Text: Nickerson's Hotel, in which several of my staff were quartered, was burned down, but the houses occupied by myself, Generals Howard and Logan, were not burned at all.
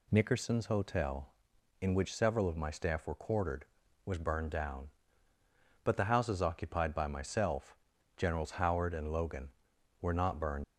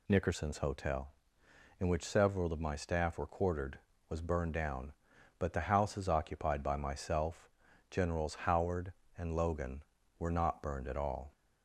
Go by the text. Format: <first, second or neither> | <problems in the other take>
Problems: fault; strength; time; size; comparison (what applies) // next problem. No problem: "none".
second | stops before "at all"; at 10.6 s